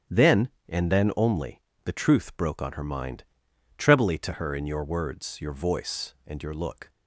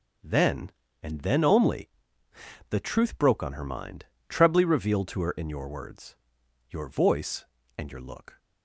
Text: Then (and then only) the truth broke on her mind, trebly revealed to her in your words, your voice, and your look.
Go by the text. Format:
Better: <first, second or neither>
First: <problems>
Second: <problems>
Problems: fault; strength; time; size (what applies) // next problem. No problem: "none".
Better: second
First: starts louder than the rest; strong; until 1.3 s; 9.5 dB // skips "revealed"; at 4.1 s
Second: none